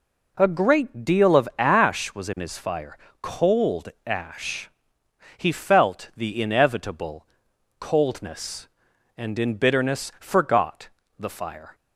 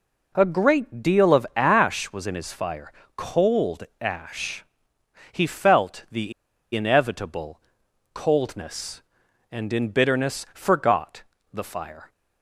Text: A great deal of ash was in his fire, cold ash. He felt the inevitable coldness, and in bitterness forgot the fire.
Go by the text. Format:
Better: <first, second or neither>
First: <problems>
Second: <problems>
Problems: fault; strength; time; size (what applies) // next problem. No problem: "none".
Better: first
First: pauses between "cold" and "ash"; slight; at 3.8 s; 0.18 s long // pauses between "inevitable" and "coldness"; noticeable; at 7.2 s; 0.54 s long // pauses between "forgot" and "the"; slight; at 10.8 s; 0.30 s long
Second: pauses between "cold" and "ash"; slight; at 3.8 s; 0.18 s long // pauses between "the" and "inevitable"; at 6.3 s; 0.42 s long // pauses between "inevitable" and "coldness"; noticeable; at 7.6 s; 0.54 s long // pauses between "forgot" and "the"; slight; at 11.2 s; 0.30 s long